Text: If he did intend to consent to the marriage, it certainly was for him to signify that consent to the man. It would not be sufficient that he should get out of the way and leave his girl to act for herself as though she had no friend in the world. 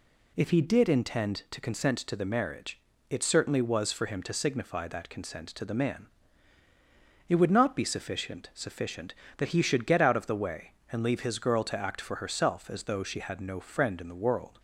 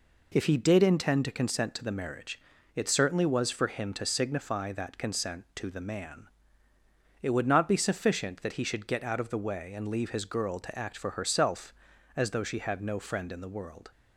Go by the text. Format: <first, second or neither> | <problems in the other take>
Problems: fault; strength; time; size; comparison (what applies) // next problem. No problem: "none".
second | says "sufficient" twice; at 8.5 s